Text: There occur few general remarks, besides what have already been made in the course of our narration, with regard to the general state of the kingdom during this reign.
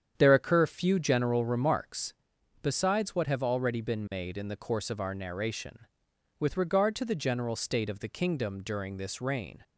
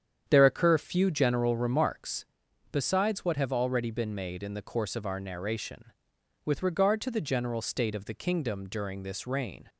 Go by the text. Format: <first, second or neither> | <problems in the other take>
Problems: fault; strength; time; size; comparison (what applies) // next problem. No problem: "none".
neither | starts louder than the rest; strong; the same in both